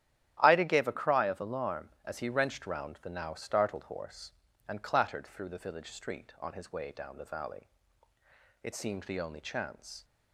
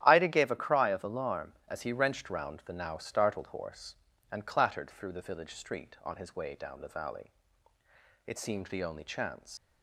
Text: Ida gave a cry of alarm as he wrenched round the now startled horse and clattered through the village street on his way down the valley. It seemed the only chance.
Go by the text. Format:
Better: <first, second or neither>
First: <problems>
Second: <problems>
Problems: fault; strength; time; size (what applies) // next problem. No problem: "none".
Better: first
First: starts louder than the rest; strong; until 1.4 s; 11.5 dB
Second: starts louder than the rest; strong; until 1.0 s; 11.5 dB // leaves "chance" unfinished; at 9.5 s; 105 ms